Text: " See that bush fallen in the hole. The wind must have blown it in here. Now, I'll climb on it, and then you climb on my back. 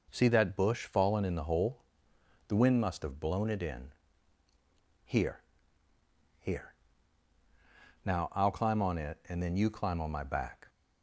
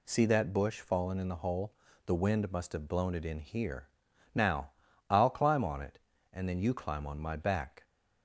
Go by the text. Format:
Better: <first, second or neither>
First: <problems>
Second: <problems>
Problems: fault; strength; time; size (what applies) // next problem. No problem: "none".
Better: second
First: pauses between "in" and "here"; at 3.9 s; 1.1 s long // says "here" twice; at 6.3 s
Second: none